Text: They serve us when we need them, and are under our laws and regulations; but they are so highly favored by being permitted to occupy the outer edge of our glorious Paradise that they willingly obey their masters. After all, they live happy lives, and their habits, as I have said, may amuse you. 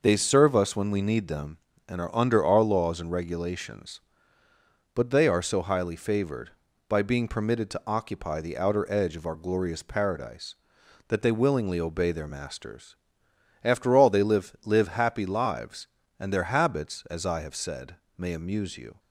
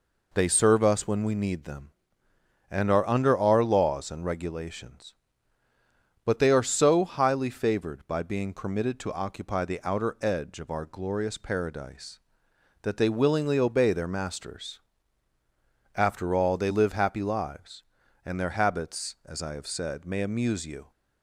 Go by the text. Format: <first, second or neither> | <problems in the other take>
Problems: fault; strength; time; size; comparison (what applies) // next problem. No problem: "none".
second | says "live" twice; at 14.6 s